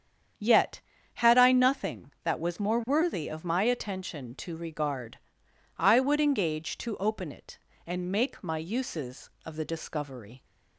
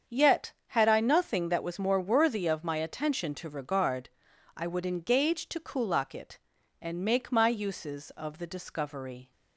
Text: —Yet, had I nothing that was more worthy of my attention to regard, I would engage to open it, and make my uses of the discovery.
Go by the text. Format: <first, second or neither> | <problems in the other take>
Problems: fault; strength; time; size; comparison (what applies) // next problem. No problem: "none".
first | starts louder than the rest; strong; until 1.2 s; 7.5 dB; strong in the first // says "kulak" for "open"; at 5.5 s